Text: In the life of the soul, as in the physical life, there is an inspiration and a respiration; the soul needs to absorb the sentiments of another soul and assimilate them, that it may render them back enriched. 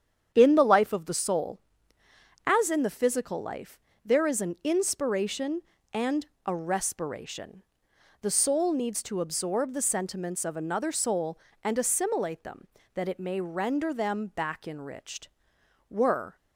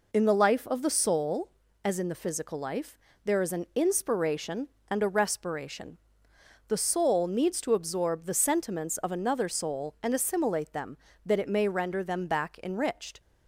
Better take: second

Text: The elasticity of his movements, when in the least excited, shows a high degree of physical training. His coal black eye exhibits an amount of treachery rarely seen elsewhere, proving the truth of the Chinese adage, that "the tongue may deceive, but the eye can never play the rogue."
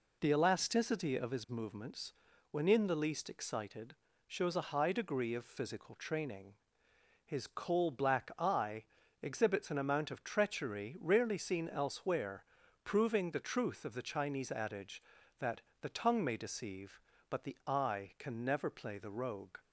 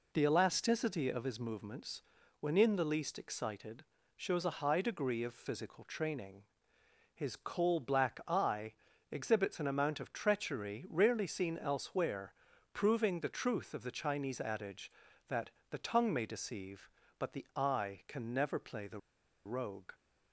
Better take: first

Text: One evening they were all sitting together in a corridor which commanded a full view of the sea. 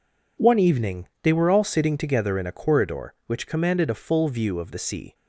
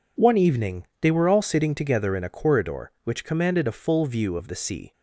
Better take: neither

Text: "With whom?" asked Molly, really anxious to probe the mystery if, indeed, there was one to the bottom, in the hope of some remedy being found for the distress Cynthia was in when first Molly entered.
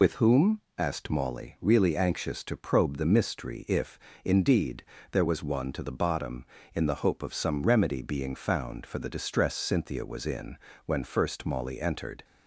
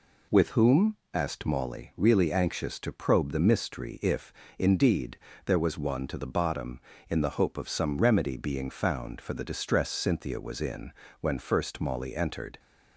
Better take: second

